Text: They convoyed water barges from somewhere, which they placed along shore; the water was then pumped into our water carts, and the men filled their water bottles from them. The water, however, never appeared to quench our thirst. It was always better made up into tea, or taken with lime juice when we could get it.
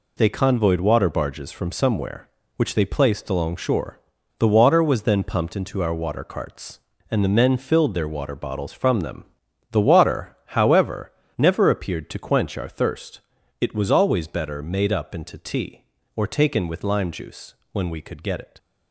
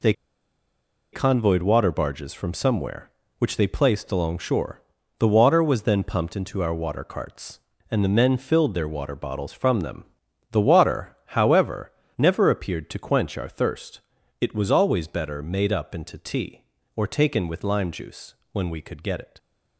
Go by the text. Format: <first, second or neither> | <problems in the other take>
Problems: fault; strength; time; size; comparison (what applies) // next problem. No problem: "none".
first | pauses between "They" and "convoyed"; at 0.1 s; 1.0 s long // pauses between "juice" and "when"; slight; at 18.3 s; 0.18 s long; slight in the first